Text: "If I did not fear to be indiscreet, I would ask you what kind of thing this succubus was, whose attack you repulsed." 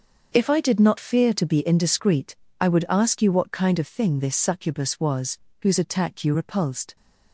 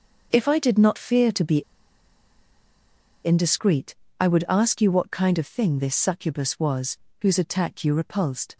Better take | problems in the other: first | starts louder than the rest; until 1.3 s; 6.5 dB; also in the first // pauses between "be" and "indiscreet"; strong; at 1.6 s; 1.6 s long

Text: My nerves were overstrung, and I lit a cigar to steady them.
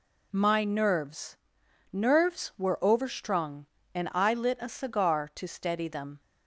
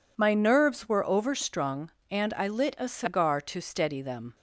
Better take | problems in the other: second | says "nerves" twice; at 1.9 s

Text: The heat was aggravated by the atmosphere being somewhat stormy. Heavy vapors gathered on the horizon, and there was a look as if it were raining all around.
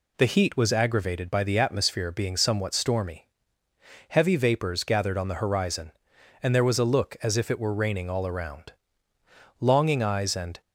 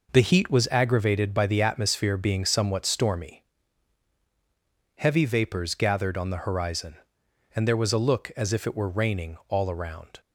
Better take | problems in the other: second | goes on to say "Longing eyes and"; noticeable; from 9.6 s on; 1.0 s long

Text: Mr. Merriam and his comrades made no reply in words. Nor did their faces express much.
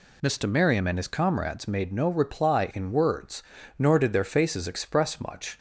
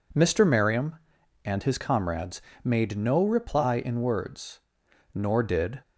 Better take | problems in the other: first | pauses between "comrades" and "made"; slight; at 2.4 s; 0.22 s long // stops before "their faces express much"; at 5.8 s

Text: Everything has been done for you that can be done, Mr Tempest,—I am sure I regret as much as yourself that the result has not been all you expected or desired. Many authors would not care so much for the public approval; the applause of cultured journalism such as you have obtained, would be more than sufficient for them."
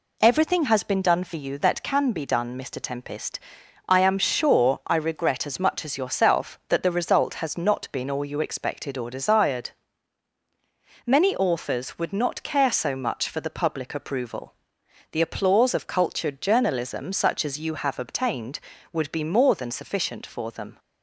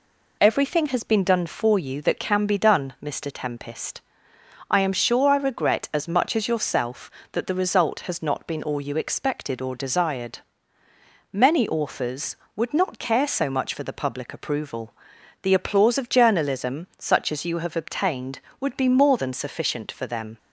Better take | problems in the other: first | skips "cultured"; at 16.0 s

